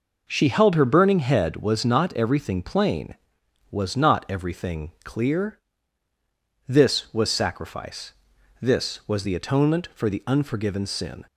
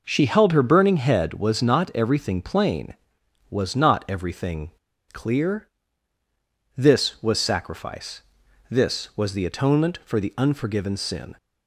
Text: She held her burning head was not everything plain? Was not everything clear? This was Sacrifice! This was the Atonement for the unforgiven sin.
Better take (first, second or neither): first